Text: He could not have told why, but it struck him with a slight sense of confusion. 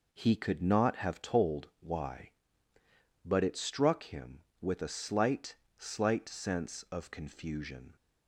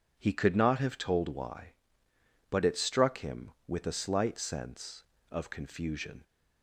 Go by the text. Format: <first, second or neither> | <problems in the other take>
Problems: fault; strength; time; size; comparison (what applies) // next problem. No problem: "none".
second | says "slight" twice; at 5.7 s